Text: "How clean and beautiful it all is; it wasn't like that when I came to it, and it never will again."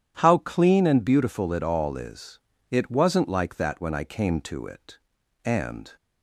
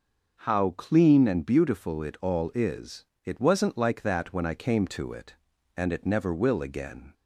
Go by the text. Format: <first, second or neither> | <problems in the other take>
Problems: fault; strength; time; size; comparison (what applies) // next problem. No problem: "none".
second | stops before "it never will again"; at 5.9 s